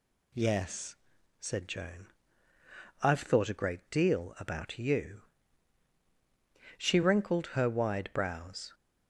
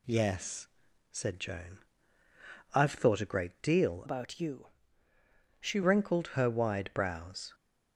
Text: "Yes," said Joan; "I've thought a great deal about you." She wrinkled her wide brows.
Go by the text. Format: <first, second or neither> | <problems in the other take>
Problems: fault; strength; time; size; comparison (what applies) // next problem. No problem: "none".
first | changes voice from "about" to "She"; from 4.0 to 5.8 s; 1.8 s long